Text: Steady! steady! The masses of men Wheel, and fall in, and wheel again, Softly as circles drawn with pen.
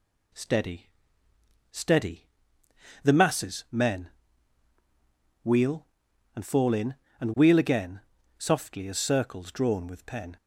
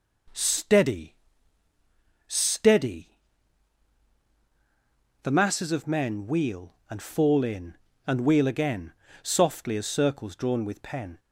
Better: second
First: skips "of"; at 3.6 s // pauses between "men" and "Wheel"; strong; at 4.0 s; 1.3 s long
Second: none

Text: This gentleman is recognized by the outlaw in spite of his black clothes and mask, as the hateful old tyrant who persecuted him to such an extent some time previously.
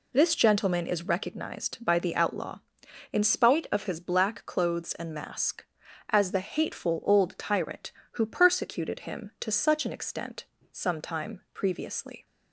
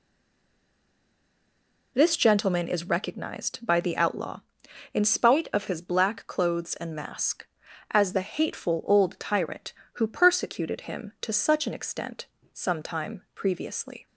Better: first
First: pauses between "extent" and "some"; slight; at 10.4 s; 0.30 s long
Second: stays silent before the first word; noticeable; until 1.9 s; 1.9 s long // pauses between "extent" and "some"; slight; at 12.2 s; 0.30 s long

